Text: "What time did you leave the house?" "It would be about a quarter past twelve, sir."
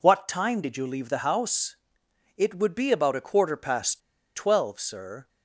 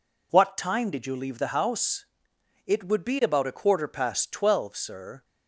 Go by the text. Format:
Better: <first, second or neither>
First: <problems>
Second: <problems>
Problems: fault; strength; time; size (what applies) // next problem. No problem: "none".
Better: second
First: pauses between "past" and "twelve"; slight; at 3.9 s; 0.35 s long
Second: none